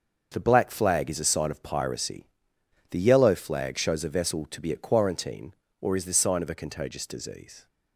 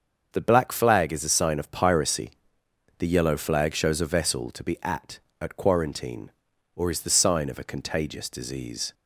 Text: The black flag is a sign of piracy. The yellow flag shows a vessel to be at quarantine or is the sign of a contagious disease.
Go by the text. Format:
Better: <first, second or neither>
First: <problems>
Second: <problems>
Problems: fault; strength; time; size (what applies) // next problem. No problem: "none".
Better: first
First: starts louder than the rest; until 1.3 s; 6.5 dB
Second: starts louder than the rest; until 1.3 s; 6.5 dB // says "at" twice; at 5.4 s